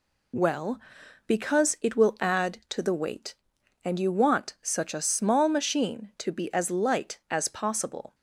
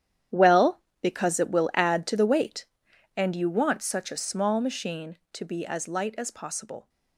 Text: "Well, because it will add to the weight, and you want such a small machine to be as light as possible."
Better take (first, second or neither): first